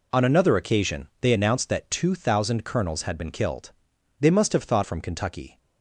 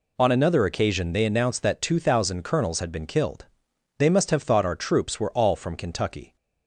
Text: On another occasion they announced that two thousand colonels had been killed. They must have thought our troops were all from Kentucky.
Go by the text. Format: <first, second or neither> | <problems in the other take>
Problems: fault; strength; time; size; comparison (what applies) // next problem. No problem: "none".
second | skips "our troops were all"; at 4.8 s